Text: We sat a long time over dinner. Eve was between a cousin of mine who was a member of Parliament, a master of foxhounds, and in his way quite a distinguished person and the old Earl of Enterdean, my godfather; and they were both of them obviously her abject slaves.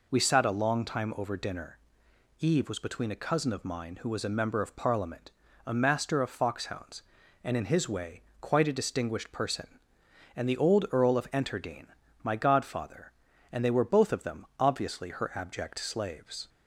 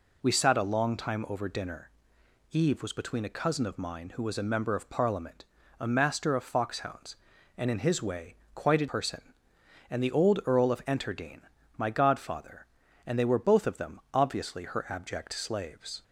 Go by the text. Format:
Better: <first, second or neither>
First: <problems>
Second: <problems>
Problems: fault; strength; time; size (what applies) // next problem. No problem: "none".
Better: first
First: pauses between "way" and "quite"; slight; at 8.2 s; 0.22 s long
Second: pauses between "way" and "quite"; slight; at 8.3 s; 0.22 s long // skips "distinguished"; at 8.8 s